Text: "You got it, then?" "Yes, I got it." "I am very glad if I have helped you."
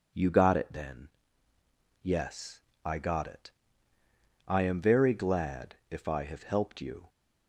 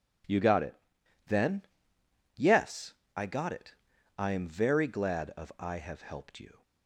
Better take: first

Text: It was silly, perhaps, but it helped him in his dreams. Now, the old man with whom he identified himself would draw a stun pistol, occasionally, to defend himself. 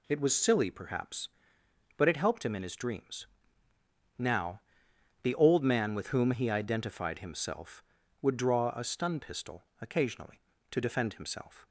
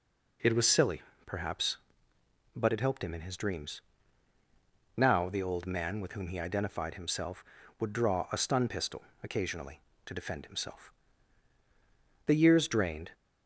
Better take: first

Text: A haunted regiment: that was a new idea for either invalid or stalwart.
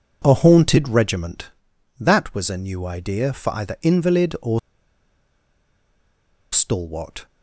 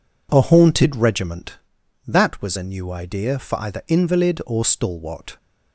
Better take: second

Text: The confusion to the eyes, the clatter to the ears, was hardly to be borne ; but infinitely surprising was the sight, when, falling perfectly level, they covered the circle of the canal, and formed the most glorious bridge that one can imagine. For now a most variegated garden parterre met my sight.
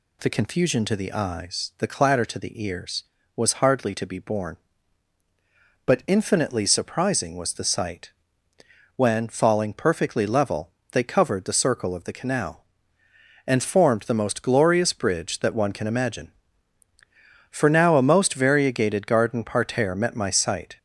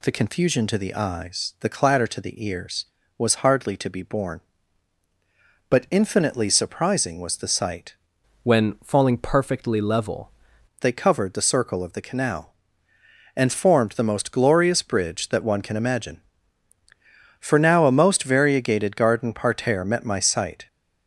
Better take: first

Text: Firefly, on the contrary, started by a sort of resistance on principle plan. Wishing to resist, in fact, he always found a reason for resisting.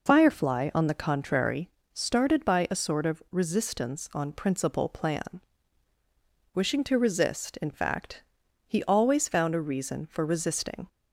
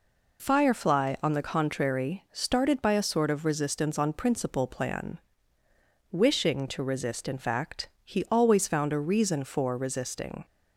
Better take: neither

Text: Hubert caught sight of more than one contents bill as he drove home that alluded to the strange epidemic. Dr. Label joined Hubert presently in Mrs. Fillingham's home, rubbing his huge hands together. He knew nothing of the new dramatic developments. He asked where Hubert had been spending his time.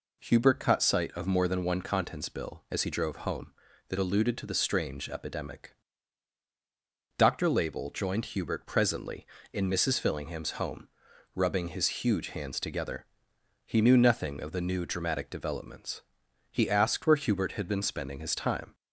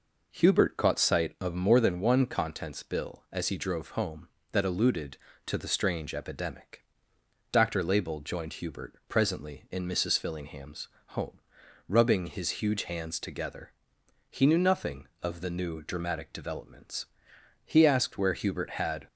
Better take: first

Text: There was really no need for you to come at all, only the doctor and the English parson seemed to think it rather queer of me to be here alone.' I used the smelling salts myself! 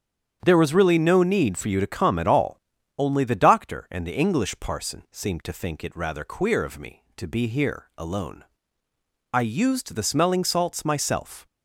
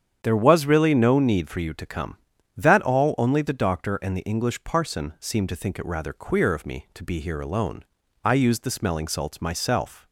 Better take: first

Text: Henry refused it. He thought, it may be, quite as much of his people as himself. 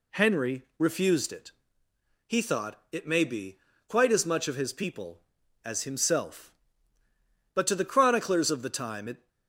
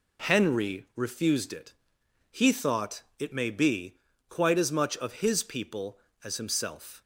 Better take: second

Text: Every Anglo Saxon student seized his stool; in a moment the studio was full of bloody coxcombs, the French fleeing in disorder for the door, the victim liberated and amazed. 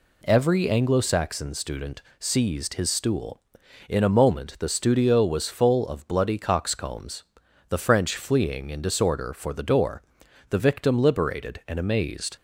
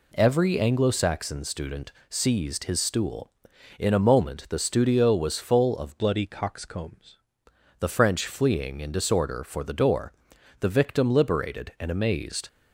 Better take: first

